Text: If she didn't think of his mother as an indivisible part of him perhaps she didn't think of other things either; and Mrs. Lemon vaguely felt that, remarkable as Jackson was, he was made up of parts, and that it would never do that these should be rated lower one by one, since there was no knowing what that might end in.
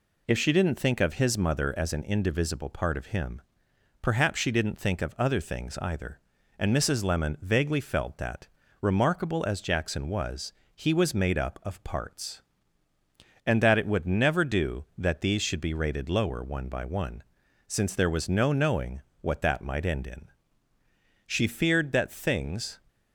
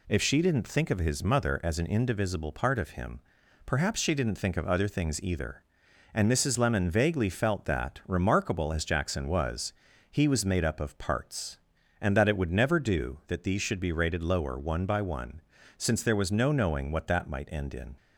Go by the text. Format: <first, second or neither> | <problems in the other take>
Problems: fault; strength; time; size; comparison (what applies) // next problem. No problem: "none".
second | pauses between "him" and "perhaps"; noticeable; at 3.4 s; 0.60 s long; also in the second // pauses between "knowing" and "what"; slight; at 19.0 s; 0.18 s long // goes on to say "She feared that things"; from 21.2 s on; 1.5 s long